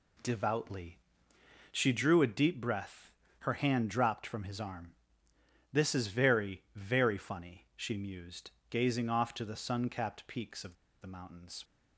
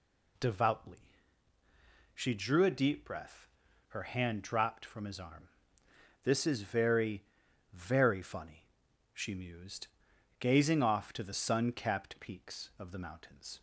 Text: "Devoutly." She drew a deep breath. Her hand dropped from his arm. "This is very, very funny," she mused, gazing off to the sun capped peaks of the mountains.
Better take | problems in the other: second | pauses between "of" and "the"; slight; at 10.7 s; 0.27 s long

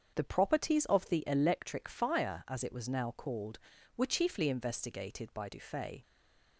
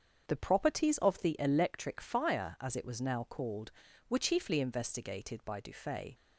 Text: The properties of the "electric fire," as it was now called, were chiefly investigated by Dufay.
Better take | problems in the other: second | starts louder than the rest; strong; until 1.1 s; 7.5 dB; strong in the second // stays silent after the last word; slight; from 6.0 s on; 0.5 s long

